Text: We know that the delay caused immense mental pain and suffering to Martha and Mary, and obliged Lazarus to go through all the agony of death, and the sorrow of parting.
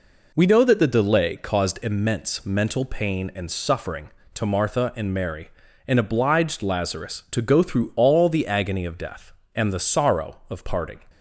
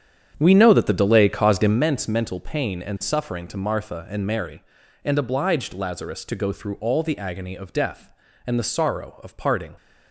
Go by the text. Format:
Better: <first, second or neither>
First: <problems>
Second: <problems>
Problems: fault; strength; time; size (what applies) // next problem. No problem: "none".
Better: first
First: none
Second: starts louder than the rest; strong; until 1.8 s; 8.5 dB